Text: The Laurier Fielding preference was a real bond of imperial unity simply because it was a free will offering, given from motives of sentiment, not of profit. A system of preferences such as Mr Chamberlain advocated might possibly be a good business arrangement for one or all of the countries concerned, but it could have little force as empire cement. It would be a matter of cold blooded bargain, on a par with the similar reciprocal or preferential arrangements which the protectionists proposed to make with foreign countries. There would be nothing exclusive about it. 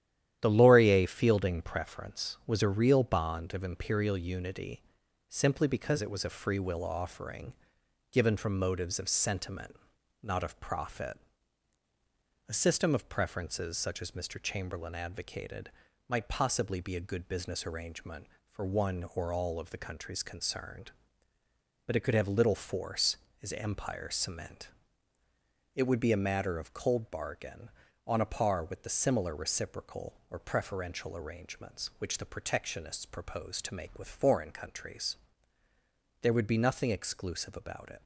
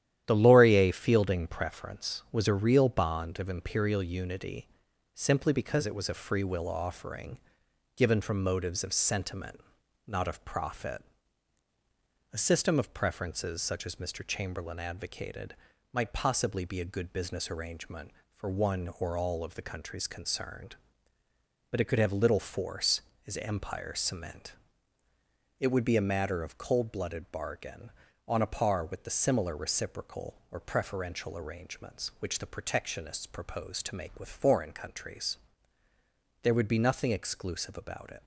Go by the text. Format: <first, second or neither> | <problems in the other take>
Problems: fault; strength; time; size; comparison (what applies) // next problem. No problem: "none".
second | starts louder than the rest; strong; until 1.4 s; 11.5 dB; strong in the second // pauses between "unity" and "simply"; noticeable; at 4.8 s; 0.46 s long; noticeable in the second // pauses between "advocated" and "might"; slight; at 15.7 s; 0.36 s long; slight in the second // skips "blooded"; at 27.0 s